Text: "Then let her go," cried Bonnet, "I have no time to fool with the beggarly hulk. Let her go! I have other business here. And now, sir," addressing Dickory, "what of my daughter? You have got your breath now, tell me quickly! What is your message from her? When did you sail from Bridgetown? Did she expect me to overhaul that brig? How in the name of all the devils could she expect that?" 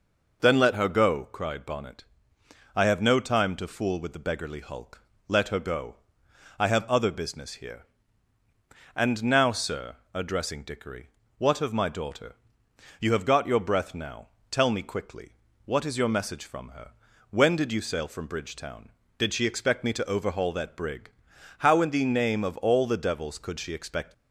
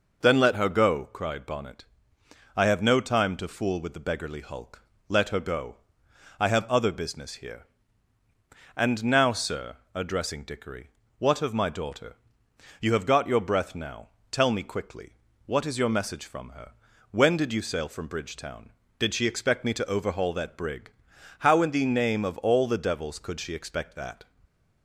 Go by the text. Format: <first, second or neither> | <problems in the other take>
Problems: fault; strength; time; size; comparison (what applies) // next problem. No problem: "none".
second | stops before "that"; at 24.1 s